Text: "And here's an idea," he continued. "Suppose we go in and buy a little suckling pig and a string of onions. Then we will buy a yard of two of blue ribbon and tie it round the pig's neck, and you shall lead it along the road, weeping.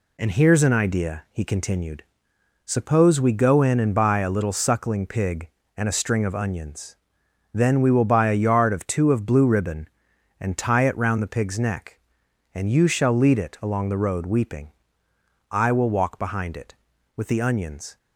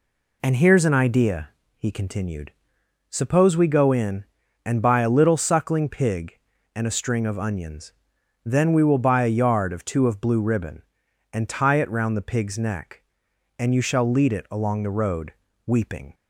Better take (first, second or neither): second